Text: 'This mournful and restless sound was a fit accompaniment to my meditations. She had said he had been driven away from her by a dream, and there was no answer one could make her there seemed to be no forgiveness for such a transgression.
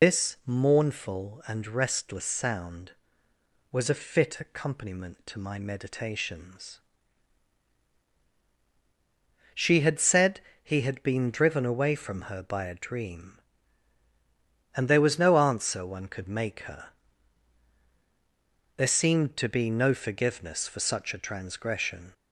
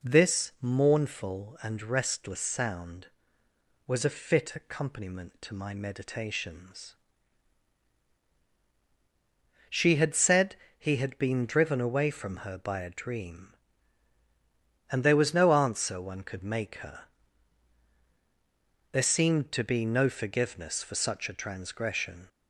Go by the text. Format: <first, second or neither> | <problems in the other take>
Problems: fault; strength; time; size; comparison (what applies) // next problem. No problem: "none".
second | loses the start of "This"; at 0.0 s; 140 ms // pauses between "said" and "he"; slight; at 10.4 s; 0.20 s long; slight in the second // pauses between "her" and "there"; strong; at 16.8 s; 1.8 s long; strong in the second